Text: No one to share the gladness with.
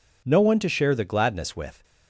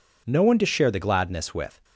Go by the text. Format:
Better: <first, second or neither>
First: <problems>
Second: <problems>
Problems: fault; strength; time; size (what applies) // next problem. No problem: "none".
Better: neither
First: none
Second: none